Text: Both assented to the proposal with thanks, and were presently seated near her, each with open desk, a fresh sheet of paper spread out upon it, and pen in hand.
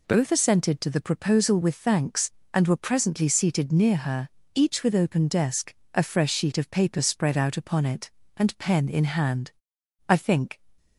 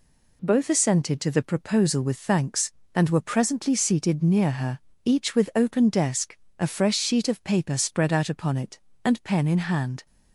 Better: second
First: goes on to say "I think"; from 10.0 s on; 0.52 s long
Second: none

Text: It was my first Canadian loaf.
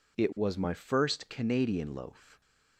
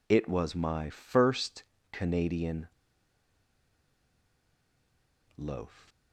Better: first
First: none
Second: pauses between "first" and "Canadian"; slight; at 1.6 s; 0.28 s long // pauses between "Canadian" and "loaf"; strong; at 2.6 s; 2.6 s long

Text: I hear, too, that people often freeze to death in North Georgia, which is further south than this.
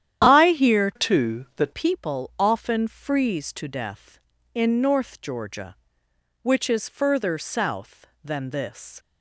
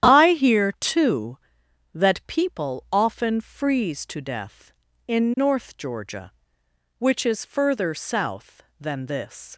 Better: second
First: starts louder than the rest; strong; until 1.2 s; 10.5 dB // changes voice from "too" to "that"; from 0.9 to 1.7 s; 0.8 s long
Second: starts louder than the rest; strong; until 1.1 s; 10.5 dB

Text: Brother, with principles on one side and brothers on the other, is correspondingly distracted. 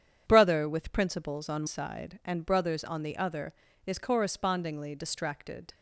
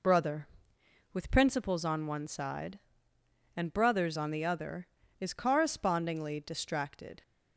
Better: second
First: starts louder than the rest; strong; until 1.2 s; 8.5 dB // skips "one"; at 1.6 s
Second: none

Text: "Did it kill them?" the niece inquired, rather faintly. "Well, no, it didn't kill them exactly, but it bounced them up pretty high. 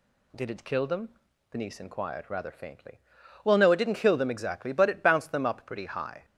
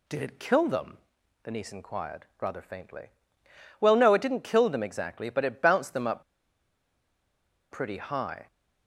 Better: first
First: none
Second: pauses between "up" and "pretty"; strong; at 6.2 s; 1.4 s long

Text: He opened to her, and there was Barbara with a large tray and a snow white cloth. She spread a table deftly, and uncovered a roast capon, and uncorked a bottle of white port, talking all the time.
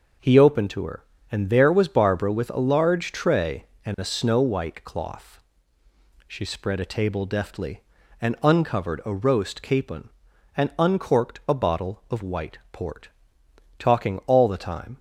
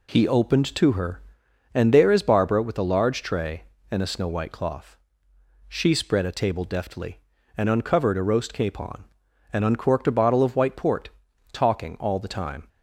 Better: first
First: none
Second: says "is" for "was"; at 2.0 s

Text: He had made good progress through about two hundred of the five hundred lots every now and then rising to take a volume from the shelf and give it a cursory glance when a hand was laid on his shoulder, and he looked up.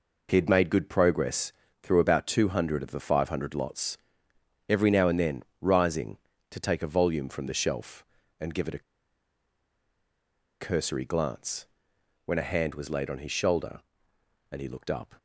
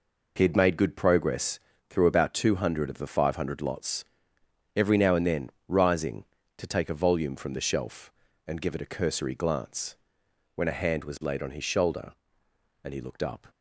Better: second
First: pauses between "progress" and "through"; slight; at 1.5 s; 0.30 s long // pauses between "lots" and "every"; noticeable; at 3.9 s; 0.70 s long // pauses between "then" and "rising"; slight; at 5.4 s; 0.18 s long // pauses between "a" and "cursory"; strong; at 8.8 s; 1.8 s long // pauses between "glance" and "when"; noticeable; at 11.6 s; 0.58 s long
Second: pauses between "progress" and "through"; slight; at 1.5 s; 0.30 s long // pauses between "lots" and "every"; noticeable; at 4.0 s; 0.70 s long // pauses between "then" and "rising"; slight; at 5.4 s; 0.18 s long // pauses between "glance" and "when"; noticeable; at 9.9 s; 0.58 s long

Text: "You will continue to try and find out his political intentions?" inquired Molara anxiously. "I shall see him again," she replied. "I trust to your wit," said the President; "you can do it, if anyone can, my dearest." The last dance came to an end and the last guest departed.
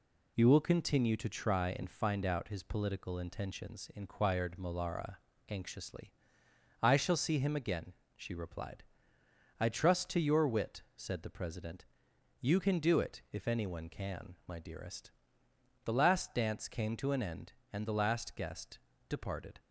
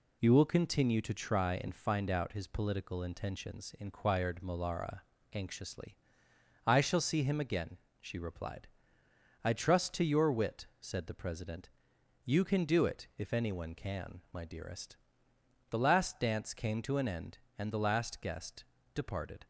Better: neither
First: pauses between "Molara" and "anxiously"; slight; at 5.1 s; 0.30 s long // pauses between "guest" and "departed"; slight; at 18.7 s; 0.30 s long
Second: pauses between "Molara" and "anxiously"; slight; at 5.0 s; 0.30 s long // pauses between "guest" and "departed"; slight; at 18.6 s; 0.30 s long

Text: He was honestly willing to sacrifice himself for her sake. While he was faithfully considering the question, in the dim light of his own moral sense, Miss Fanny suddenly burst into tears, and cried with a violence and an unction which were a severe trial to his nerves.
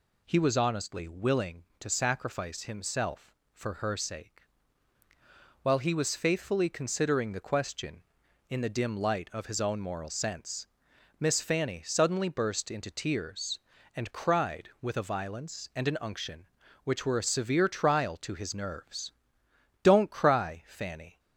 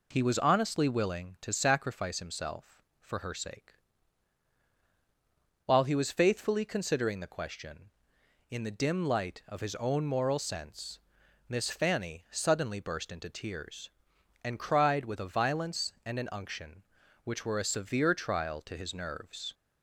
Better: second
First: goes on to say "Don't cry Fanny"; from 19.8 s on; 1.3 s long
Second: none

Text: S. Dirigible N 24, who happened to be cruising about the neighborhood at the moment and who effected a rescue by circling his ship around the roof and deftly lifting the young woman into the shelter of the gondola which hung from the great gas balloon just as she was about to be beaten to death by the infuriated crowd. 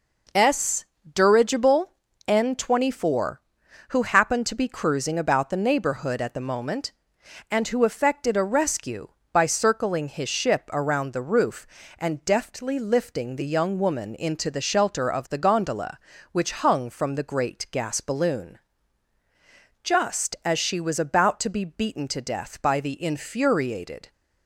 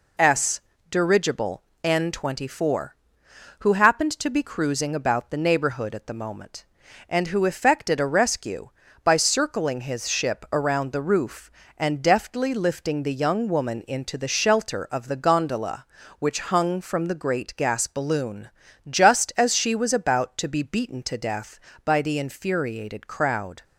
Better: second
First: pauses between "Dirigible" and "N"; slight; at 1.9 s; 0.34 s long // pauses between "balloon" and "just"; at 18.5 s; 1.2 s long // stops before "crowd"; at 24.1 s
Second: pauses between "Dirigible" and "N"; slight; at 1.6 s; 0.22 s long // pauses between "balloon" and "just"; at 18.4 s; 0.40 s long

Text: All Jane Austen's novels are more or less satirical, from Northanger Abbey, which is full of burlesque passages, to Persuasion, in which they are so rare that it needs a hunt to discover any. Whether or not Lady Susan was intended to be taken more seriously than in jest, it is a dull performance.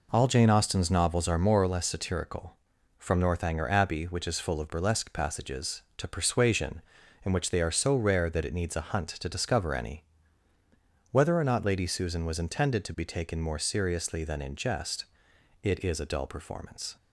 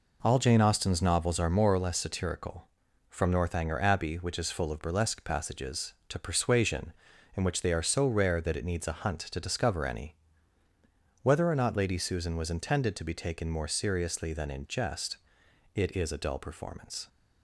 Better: neither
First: none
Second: none

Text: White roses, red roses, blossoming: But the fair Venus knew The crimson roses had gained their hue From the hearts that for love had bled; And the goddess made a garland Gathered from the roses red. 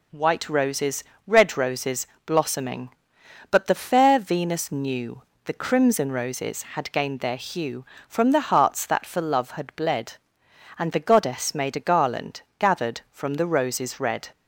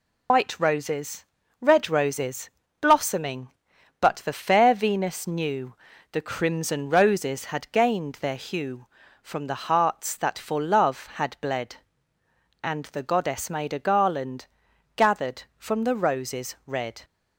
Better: first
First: pauses between "knew" and "The"; slight; at 5.2 s; 0.24 s long // pauses between "garland" and "Gathered"; slight; at 12.4 s; 0.18 s long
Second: loses the start of "White"; at 0.2 s; 90 ms // pauses between "knew" and "The"; slight; at 5.7 s; 0.34 s long // pauses between "garland" and "Gathered"; noticeable; at 14.4 s; 0.50 s long

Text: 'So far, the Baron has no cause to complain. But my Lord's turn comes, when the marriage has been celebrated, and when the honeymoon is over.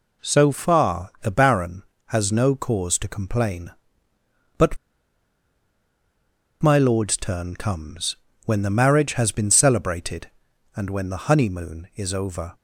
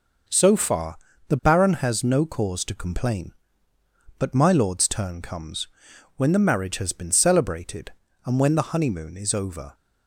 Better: second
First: pauses between "But" and "my"; strong; at 4.7 s; 1.8 s long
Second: none

